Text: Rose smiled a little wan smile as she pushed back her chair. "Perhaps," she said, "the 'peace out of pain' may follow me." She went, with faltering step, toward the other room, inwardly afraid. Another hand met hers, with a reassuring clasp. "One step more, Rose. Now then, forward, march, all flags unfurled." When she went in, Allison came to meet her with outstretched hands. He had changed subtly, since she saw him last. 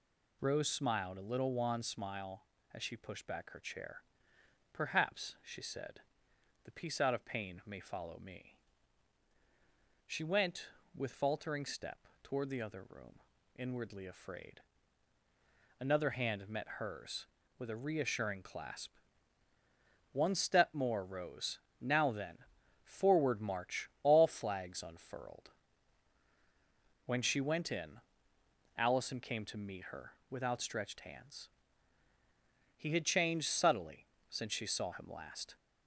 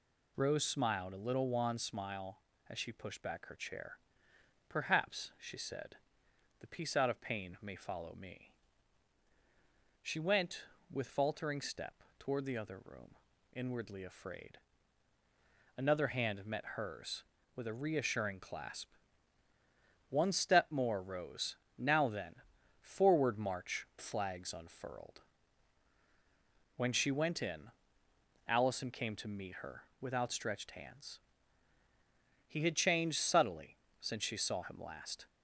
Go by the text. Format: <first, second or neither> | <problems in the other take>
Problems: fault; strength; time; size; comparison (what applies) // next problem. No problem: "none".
first | skips "all"; at 23.9 s